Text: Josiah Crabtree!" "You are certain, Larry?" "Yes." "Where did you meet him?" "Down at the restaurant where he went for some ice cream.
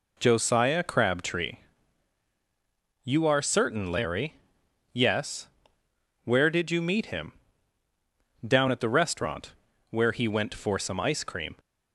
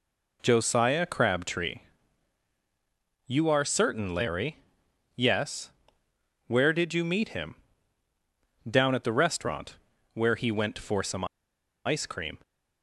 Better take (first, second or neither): first